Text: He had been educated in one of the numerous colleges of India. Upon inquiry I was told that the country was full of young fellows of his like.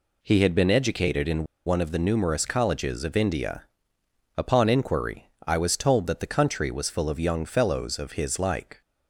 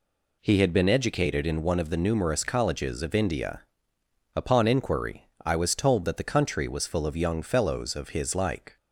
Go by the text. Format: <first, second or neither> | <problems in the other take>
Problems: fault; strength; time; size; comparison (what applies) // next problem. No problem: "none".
second | pauses between "in" and "one"; slight; at 1.4 s; 0.21 s long // pauses between "inquiry" and "I"; slight; at 5.2 s; 0.18 s long; slight in the second